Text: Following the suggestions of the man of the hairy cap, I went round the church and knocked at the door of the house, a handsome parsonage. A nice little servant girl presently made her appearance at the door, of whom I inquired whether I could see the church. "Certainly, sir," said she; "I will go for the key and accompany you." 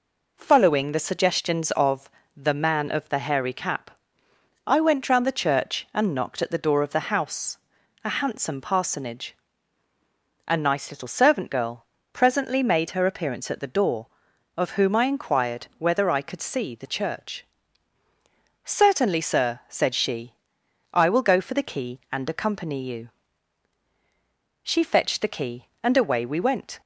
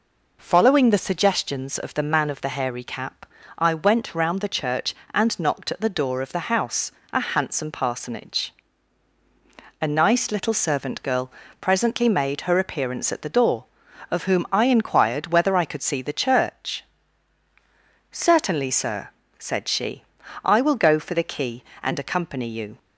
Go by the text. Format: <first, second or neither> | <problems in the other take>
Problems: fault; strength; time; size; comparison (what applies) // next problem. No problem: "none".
second | pauses between "of" and "the"; slight; at 2.1 s; 0.26 s long // pauses between "girl" and "presently"; slight; at 11.8 s; 0.26 s long; slight in the second // goes on to say "She fetched the key and away we went"; strong; from 24.6 s on; 2.1 s long